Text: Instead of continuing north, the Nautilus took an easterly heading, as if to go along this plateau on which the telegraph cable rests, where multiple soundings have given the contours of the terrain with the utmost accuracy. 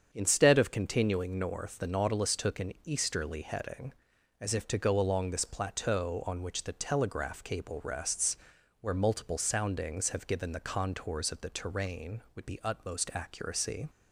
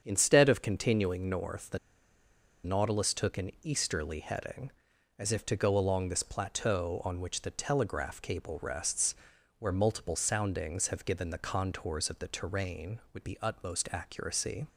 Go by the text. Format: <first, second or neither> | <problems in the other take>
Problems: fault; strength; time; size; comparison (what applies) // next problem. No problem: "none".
first | starts louder than the rest; strong; until 1.0 s; 7.5 dB; strong in the first // pauses between "the" and "Nautilus"; noticeable; at 1.7 s; 0.85 s long